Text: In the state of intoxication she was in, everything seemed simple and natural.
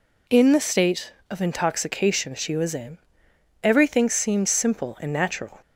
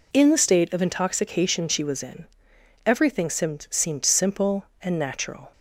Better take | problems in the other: first | says "seemed" twice; at 3.6 s

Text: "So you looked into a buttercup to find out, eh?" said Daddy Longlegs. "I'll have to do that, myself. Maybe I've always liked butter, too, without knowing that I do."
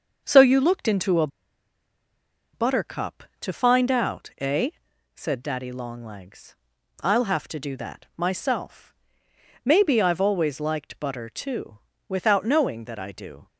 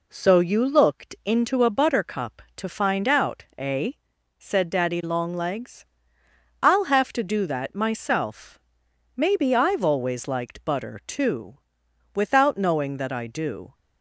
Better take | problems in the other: second | starts louder than the rest; until 1.2 s; 6.5 dB // pauses between "a" and "buttercup"; strong; at 1.2 s; 1.2 s long

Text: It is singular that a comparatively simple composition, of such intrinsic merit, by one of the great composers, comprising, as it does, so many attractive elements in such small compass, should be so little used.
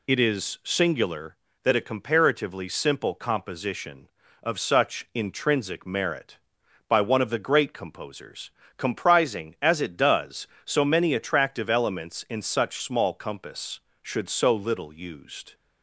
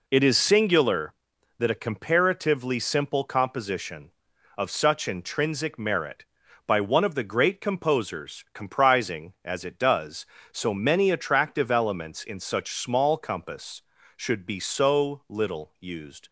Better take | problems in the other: second | skips "be"; at 14.2 s

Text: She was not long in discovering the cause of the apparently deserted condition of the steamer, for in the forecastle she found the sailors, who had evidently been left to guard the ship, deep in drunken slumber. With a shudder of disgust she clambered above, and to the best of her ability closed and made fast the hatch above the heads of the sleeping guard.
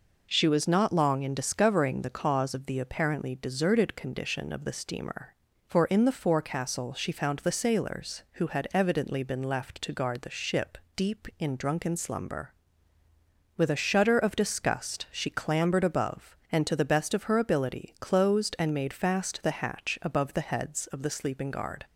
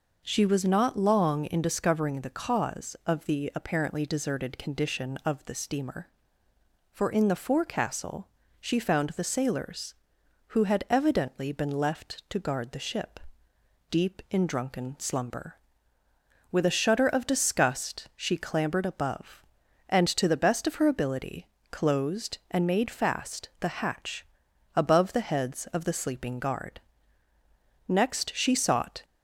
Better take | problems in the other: first | pauses between "forecastle" and "she"; slight; at 8.2 s; 0.30 s long // pauses between "ability" and "closed"; slight; at 21.4 s; 0.22 s long // pauses between "hatch" and "above"; noticeable; at 24.2 s; 0.48 s long // goes on to say "Next she sought"; noticeable; from 27.8 s on; 1.1 s long

